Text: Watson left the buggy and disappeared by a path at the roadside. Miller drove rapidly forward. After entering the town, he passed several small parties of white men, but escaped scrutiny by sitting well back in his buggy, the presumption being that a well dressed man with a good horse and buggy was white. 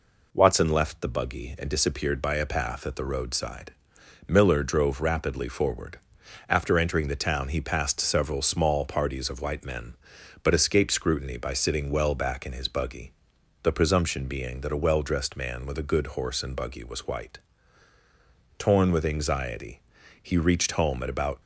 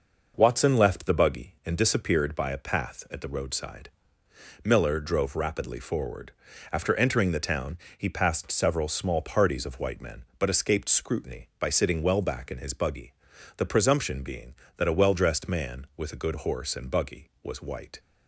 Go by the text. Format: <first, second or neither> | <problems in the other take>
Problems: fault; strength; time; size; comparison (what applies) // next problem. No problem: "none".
second | goes on to say "Torn with anxiety he reached home at about"; strong; from 18.5 s on; 2.8 s long